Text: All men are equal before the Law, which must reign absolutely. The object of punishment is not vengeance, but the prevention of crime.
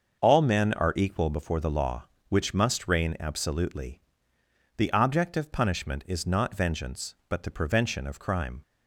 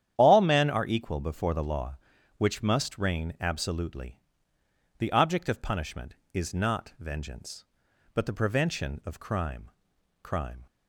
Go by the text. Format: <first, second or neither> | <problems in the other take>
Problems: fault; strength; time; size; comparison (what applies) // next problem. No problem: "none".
first | starts louder than the rest; strong; until 1.1 s; 10 dB; also in the first // says "crime" twice; at 10.2 s